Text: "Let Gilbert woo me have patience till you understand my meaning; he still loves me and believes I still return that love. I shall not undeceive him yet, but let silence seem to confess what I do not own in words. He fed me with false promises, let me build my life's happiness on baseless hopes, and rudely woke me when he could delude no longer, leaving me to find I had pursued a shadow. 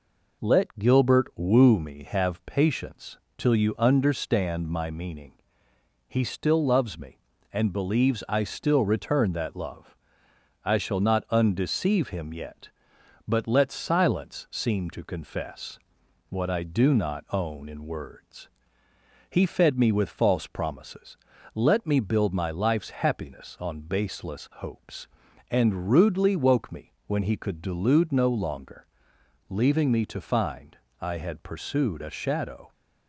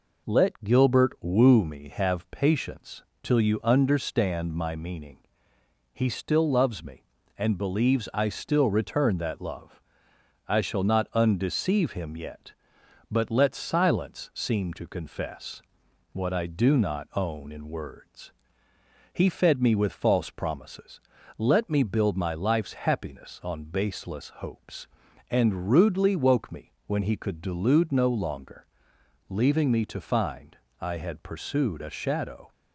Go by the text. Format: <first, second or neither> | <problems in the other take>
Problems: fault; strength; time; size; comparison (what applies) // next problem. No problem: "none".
neither | pauses between "patience" and "till"; slight; the same in both // pauses between "confess" and "what"; noticeable; the same in both // pauses between "find" and "I"; slight; the same in both